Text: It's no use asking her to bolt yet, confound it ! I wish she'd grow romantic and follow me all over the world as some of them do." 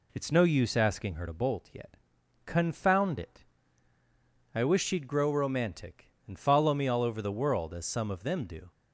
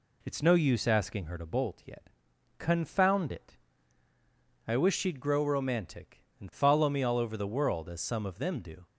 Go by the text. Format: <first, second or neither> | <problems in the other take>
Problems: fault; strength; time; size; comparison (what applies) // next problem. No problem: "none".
neither | none